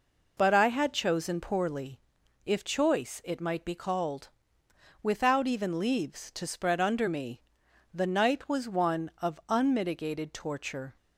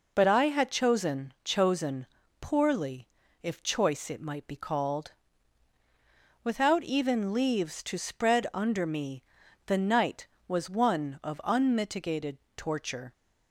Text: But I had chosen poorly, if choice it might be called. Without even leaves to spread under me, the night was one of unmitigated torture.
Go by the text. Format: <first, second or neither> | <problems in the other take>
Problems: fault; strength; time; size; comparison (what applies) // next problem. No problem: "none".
first | says "chosen" twice; at 1.4 s // pauses between "unmitigated" and "torture"; slight; at 12.3 s; 0.18 s long